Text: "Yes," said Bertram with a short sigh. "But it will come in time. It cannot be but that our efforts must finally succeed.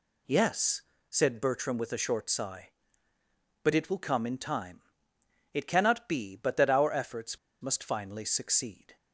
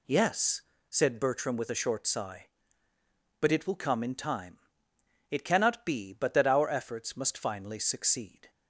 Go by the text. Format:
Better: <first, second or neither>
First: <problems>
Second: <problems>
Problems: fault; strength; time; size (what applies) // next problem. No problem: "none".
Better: second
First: pauses between "efforts" and "must"; slight; at 7.3 s; 0.23 s long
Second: none